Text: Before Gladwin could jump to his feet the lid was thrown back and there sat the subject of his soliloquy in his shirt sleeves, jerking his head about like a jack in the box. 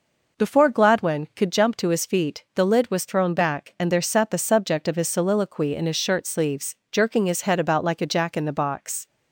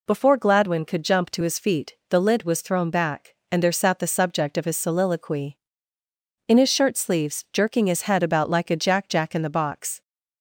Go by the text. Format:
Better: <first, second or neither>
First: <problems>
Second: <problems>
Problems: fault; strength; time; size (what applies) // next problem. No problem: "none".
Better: first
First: none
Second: says "jack" twice; at 9.0 s